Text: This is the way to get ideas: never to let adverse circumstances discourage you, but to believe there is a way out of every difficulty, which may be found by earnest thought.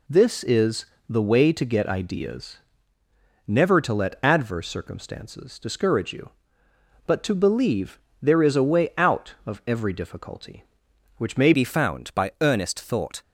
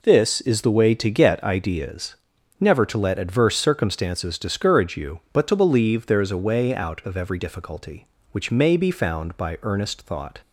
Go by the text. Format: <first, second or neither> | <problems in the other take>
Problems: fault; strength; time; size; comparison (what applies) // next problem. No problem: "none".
second | pauses between "is" and "the"; slight; at 0.8 s; 0.22 s long // pauses between "believe" and "there"; slight; at 7.9 s; 0.24 s long // changes voice at "be"; from 11.5 s on; 1.7 s long